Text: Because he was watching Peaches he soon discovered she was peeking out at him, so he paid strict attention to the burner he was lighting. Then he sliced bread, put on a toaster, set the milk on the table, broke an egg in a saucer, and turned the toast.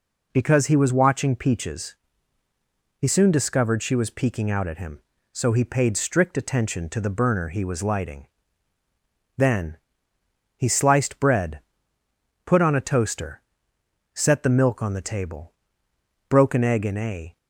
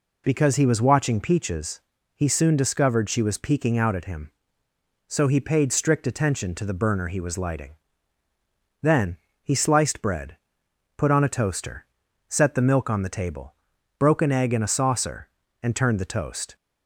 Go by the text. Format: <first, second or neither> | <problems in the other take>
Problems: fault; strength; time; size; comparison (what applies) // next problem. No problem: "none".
second | pauses between "Peaches" and "he"; at 1.9 s; 1.0 s long; slight in the second // pauses between "Then" and "he"; noticeable; at 9.7 s; 0.80 s long; slight in the second // stops before "saucer and turned the toast"; at 17.3 s